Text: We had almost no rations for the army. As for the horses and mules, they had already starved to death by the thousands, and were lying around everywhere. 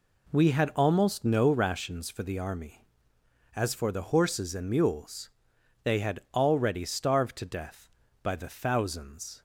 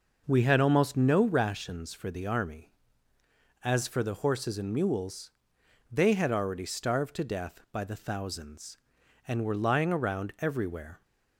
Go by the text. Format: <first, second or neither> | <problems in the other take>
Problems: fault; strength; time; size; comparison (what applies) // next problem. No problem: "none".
second | pauses between "had" and "already"; slight; at 6.1 s; 0.16 s long // stops before "and were lying around everywhere"; at 9.3 s